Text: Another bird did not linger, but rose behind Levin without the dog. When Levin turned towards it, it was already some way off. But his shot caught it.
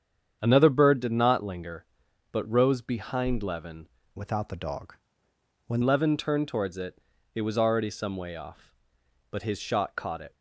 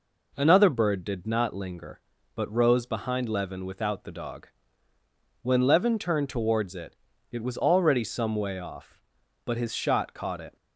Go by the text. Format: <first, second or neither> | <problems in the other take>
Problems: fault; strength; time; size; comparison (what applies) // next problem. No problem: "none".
second | starts louder than the rest; strong; until 1.4 s; 8 dB // changes voice from "without" to "When"; from 4.1 to 5.8 s; 1.7 s long